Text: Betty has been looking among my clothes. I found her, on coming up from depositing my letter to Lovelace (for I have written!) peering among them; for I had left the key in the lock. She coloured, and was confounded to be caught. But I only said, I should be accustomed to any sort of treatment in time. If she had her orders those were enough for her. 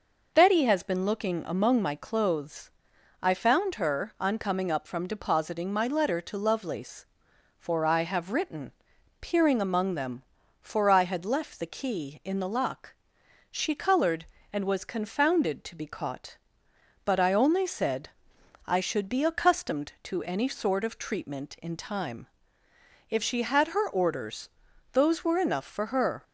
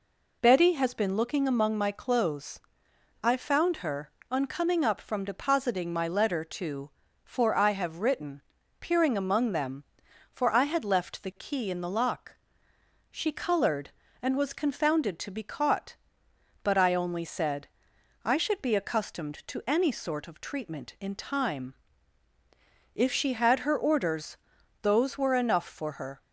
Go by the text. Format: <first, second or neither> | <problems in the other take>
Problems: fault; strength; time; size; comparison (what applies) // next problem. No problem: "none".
first | skips "Lovelace"; at 7.0 s // pauses between "orders" and "those"; noticeable; at 24.3 s; 0.46 s long; also in the first